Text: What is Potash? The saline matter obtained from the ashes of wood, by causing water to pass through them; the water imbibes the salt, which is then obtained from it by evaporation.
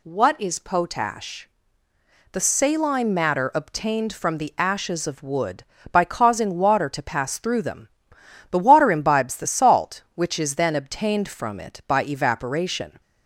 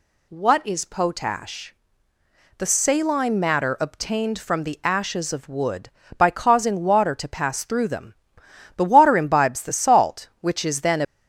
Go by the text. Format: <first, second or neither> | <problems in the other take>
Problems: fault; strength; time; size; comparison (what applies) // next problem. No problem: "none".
first | stops before "obtained from it by evaporation"; at 11.0 s